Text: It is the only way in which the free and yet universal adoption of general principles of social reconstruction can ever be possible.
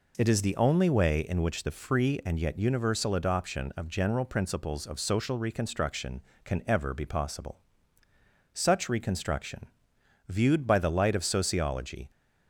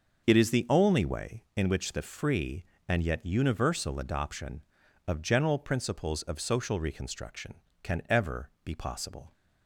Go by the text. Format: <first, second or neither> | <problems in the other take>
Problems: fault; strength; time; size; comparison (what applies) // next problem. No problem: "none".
second | goes on to say "Such reconstruction viewed by the light of Sociology"; strong; from 8.5 s on; 3.5 s long